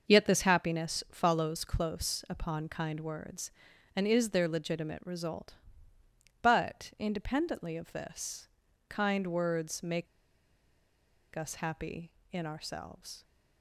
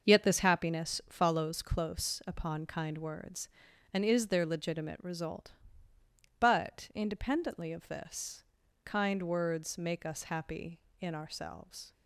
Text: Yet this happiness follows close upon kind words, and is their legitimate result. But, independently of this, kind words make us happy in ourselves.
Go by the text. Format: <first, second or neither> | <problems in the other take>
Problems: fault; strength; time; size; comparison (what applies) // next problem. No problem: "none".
second | starts louder than the rest; until 1.1 s; 6 dB; noticeable in the second // pauses between "make" and "us"; strong; at 10.0 s; 1.2 s long